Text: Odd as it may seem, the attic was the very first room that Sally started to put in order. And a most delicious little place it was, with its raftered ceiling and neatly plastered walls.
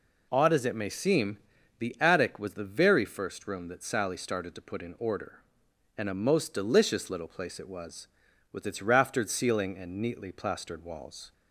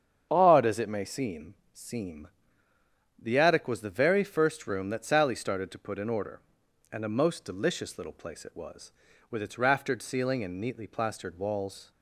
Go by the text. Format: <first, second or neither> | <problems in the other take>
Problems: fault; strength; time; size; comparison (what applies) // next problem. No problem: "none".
first | starts louder than the rest; strong; until 1.3 s; 7.5 dB // says "seem" twice; at 1.7 s